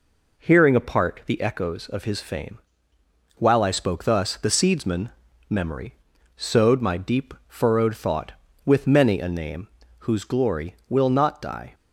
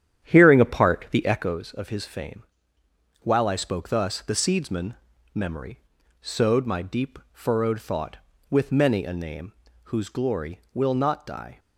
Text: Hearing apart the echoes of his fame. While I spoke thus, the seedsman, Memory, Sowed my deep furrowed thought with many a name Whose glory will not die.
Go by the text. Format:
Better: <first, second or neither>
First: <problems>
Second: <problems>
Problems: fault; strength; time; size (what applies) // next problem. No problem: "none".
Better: first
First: pauses between "name" and "Whose"; slight; at 9.6 s; 0.34 s long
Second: starts louder than the rest; strong; until 1.7 s; 10 dB // pauses between "name" and "Whose"; slight; at 9.5 s; 0.34 s long